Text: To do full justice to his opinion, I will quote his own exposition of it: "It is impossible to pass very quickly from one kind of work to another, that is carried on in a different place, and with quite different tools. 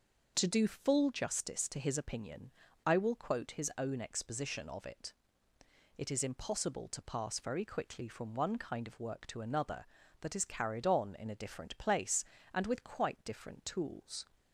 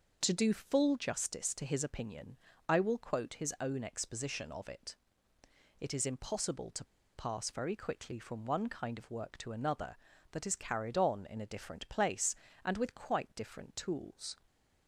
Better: first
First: none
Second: pauses between "to" and "pass"; slight; at 6.8 s; 0.29 s long

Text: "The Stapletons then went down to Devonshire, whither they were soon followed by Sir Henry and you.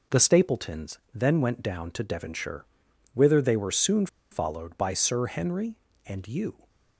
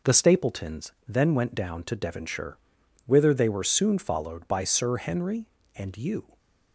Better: second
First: pauses between "Stapletons" and "then"; slight; at 0.9 s; 0.16 s long // pauses between "soon" and "followed"; slight; at 4.0 s; 0.24 s long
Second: pauses between "Stapletons" and "then"; slight; at 0.9 s; 0.16 s long

